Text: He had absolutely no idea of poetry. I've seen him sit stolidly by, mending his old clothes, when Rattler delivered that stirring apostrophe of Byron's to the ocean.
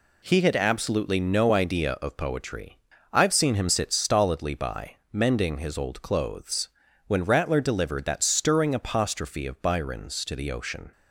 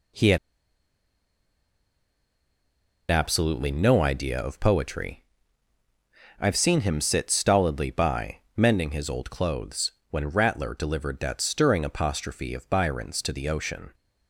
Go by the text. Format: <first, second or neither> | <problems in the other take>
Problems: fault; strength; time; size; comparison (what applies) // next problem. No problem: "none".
first | pauses between "had" and "absolutely"; strong; at 0.3 s; 2.7 s long